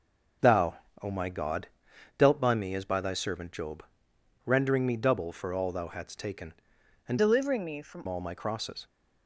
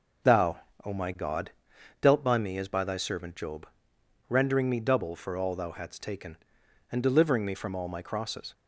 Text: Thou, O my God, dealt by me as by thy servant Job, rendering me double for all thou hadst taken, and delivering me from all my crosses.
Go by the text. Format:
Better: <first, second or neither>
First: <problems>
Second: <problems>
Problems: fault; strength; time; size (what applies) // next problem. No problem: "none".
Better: second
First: changes voice from "delivering" to "from"; from 7.1 to 8.0 s; 0.9 s long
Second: none